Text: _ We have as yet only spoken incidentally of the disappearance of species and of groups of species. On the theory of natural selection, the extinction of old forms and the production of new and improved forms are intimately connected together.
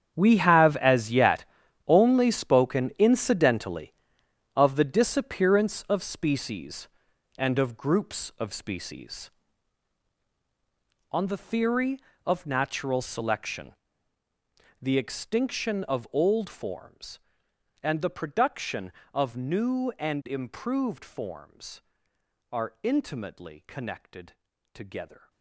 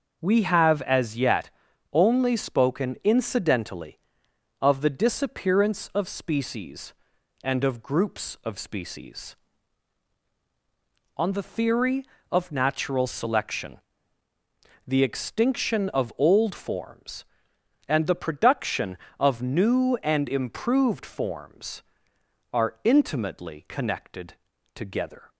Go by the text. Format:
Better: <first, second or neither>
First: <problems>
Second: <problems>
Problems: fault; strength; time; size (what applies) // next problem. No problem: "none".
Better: second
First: gets quieter; strong; throughout; 14.5 dB // starts louder than the rest; strong; until 1.1 s; 8.5 dB // pauses between "yet" and "only"; at 1.4 s; 0.42 s long // pauses between "connected" and "together"; at 24.3 s; 0.42 s long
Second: starts louder than the rest; noticeable; until 1.2 s; 6 dB // pauses between "yet" and "only"; at 1.4 s; 0.42 s long // pauses between "connected" and "together"; at 24.3 s; 0.42 s long